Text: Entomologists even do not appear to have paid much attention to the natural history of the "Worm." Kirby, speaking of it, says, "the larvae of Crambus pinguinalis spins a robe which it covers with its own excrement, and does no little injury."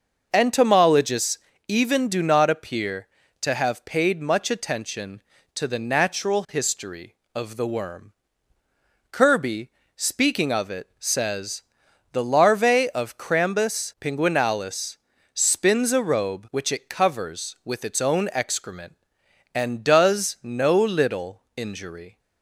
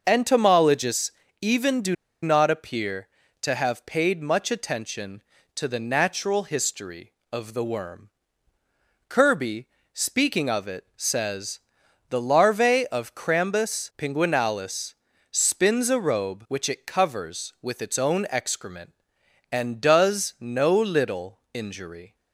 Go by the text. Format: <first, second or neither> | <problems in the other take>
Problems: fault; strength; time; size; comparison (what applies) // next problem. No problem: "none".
first | starts louder than the rest; noticeable; until 1.0 s; 6 dB; noticeable in the first // pauses between "Entomologists" and "even"; slight; at 1.1 s; 0.28 s long; slight in the first // pauses between "do" and "not"; slight; at 1.9 s; 0.28 s long // pauses between "pinguinalis" and "spins"; at 14.9 s; 0.38 s long; also in the first